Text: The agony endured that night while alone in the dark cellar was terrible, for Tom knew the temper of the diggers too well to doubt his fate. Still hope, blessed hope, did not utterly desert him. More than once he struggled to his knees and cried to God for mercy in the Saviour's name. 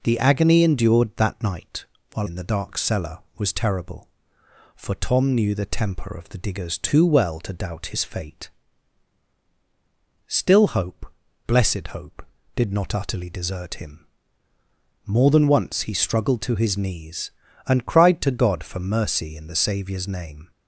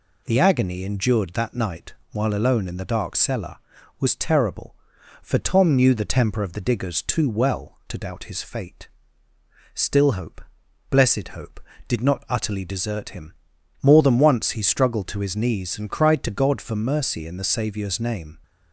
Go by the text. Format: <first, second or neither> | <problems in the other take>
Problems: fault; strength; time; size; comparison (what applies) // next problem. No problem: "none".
second | pauses between "night" and "while"; slight; at 1.8 s; 0.28 s long; slight in the second // skips "alone"; at 2.2 s